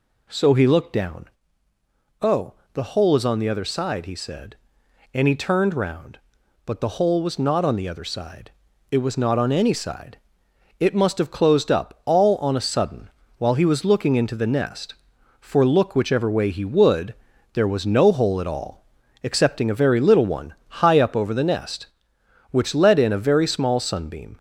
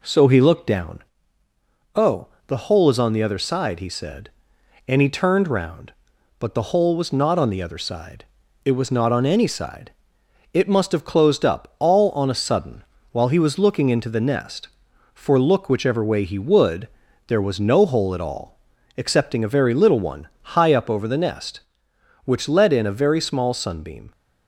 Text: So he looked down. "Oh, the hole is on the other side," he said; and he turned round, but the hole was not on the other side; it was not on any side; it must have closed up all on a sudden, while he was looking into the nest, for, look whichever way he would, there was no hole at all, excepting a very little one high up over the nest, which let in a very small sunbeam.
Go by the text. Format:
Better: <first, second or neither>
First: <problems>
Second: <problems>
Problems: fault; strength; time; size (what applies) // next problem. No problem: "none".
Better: second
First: gets louder; throughout; 3.5 dB // pauses between "one" and "high"; slight; at 20.5 s; 0.28 s long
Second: pauses between "one" and "high"; slight; at 20.2 s; 0.28 s long